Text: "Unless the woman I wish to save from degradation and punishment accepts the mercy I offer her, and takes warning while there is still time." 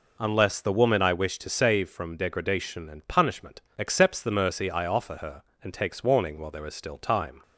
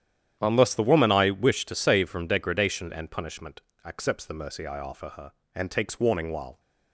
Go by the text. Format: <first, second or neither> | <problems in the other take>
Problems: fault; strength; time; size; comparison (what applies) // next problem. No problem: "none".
first | starts louder than the rest; strong; until 1.4 s; 10 dB // pauses between "punishment" and "accepts"; slight; at 3.5 s; 0.24 s long; slight in the first // stops before "there is still time"; at 6.5 s